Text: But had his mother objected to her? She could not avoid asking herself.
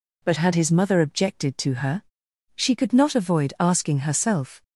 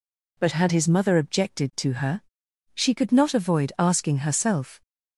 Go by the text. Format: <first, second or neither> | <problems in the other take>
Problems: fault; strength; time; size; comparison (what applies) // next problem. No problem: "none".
neither | none